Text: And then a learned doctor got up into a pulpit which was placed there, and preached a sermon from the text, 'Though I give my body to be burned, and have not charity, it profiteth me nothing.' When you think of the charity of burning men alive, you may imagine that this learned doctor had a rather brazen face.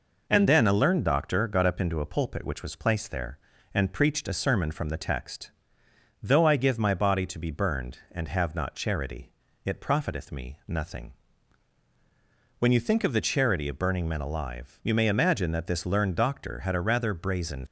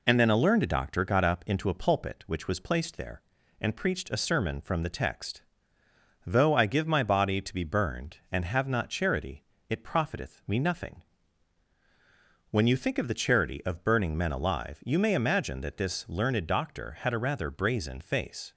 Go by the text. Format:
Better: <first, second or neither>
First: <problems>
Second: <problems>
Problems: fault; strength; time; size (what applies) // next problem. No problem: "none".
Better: second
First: stops before "face"; at 17.6 s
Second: none